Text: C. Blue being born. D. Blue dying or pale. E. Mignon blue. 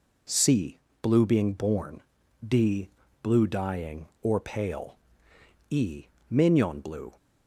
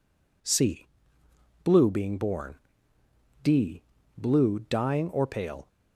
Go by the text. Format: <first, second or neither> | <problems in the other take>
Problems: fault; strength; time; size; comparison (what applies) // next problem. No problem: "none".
first | stops before "E Mignon blue"; at 5.6 s